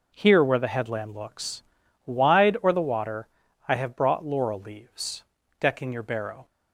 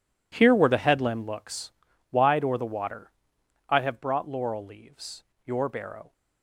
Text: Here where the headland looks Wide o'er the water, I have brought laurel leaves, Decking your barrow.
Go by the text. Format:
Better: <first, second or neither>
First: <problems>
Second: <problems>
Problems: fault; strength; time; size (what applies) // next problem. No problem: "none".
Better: first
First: pauses between "looks" and "Wide"; at 1.6 s; 0.42 s long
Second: pauses between "looks" and "Wide"; at 1.7 s; 0.40 s long // skips "Decking"; at 5.3 s